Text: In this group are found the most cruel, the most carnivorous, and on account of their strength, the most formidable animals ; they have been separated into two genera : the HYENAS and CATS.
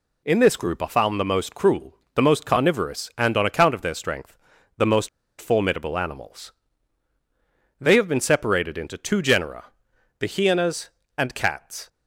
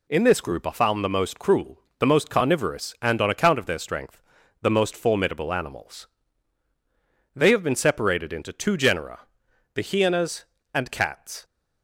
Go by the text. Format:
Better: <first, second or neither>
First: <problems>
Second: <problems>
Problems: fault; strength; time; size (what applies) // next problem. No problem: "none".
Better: second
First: pauses between "most" and "formidable"; slight; at 5.0 s; 0.30 s long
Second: none